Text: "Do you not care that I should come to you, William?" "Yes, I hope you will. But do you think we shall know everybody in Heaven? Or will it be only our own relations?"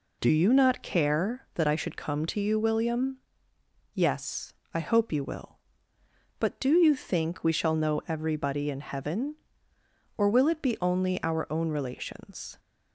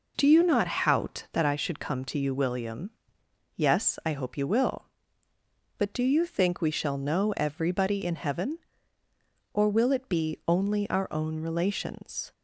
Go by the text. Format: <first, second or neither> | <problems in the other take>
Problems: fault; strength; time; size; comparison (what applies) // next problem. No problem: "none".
first | says "hout" for "care"; at 0.6 s